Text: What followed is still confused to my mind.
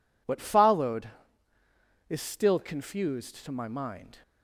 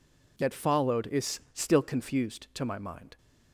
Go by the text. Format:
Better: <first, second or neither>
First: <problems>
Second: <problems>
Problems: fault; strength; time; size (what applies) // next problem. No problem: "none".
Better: first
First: none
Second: says "That" for "What"; at 0.3 s